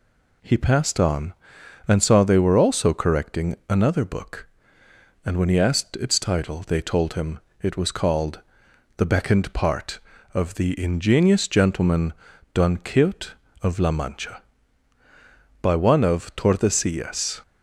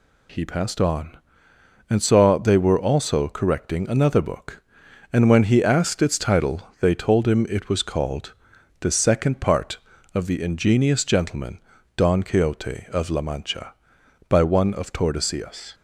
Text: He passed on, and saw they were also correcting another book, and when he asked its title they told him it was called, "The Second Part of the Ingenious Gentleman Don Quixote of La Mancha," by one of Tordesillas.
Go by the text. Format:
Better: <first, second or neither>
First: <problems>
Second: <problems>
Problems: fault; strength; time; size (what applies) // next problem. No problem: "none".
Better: second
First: pauses between "him" and "it"; slight; at 7.3 s; 0.22 s long // says "Beckoned" for "Second"; at 9.0 s // pauses between "Gentleman" and "Don"; at 12.1 s; 0.40 s long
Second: pauses between "Gentleman" and "Don"; at 11.5 s; 0.38 s long